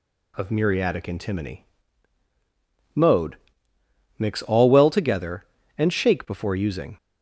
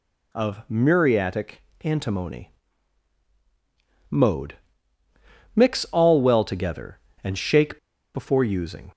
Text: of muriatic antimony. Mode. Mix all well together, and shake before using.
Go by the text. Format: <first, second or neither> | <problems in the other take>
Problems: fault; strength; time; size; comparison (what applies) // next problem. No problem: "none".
first | pauses between "muriatic" and "antimony"; slight; at 1.6 s; 0.20 s long // pauses between "shake" and "before"; at 7.7 s; 0.36 s long